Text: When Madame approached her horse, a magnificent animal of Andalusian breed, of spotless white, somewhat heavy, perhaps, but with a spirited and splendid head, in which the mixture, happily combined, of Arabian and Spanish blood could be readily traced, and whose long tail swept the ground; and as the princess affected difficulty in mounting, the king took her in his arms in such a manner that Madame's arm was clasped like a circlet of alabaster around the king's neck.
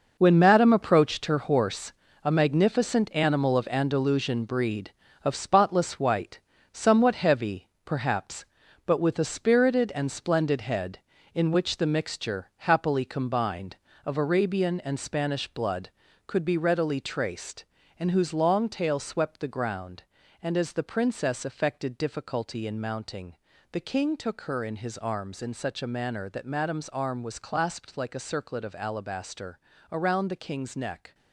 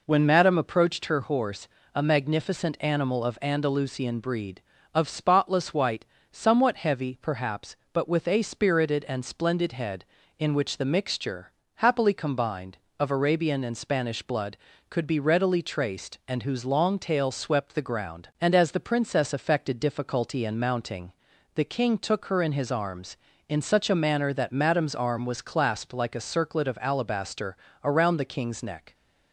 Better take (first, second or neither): second